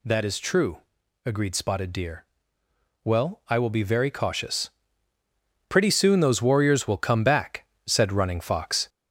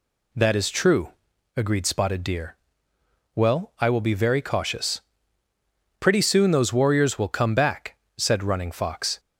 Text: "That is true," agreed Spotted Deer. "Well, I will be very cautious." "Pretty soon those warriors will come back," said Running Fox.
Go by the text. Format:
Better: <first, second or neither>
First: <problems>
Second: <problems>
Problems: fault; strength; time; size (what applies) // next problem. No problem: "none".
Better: second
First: gets louder; noticeable; throughout; 4.5 dB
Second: none